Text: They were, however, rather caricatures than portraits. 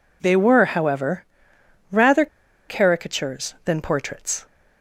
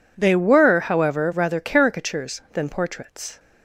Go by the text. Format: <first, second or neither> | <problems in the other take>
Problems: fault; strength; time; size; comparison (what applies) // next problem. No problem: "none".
second | pauses between "rather" and "caricatures"; at 2.2 s; 0.42 s long